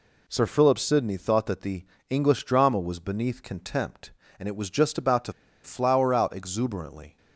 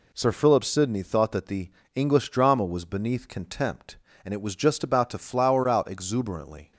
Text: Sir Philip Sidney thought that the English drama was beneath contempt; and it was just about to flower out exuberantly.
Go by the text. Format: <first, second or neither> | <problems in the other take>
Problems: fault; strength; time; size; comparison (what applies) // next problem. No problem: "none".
second | pauses between "the" and "English"; slight; at 1.8 s; 0.26 s long; slight in the second // pauses between "to" and "flower"; slight; at 5.3 s; 0.32 s long